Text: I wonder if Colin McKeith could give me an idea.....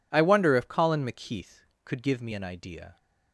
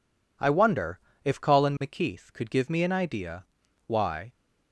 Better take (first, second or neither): first